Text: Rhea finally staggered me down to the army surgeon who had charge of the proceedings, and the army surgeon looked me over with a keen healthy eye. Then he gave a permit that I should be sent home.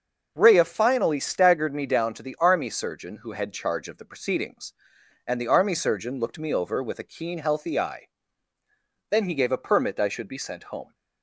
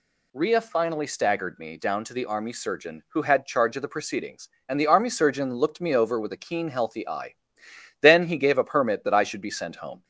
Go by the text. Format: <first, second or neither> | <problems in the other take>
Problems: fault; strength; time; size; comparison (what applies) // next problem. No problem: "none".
second | starts louder than the rest; until 1.3 s; 6 dB // skips "that"; at 9.9 s